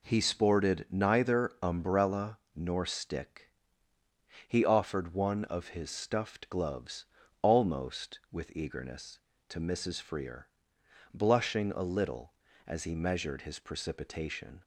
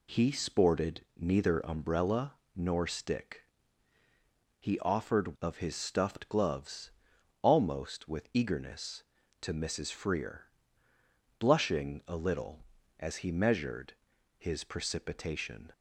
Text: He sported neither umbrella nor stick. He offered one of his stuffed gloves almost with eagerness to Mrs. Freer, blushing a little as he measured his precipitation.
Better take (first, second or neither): first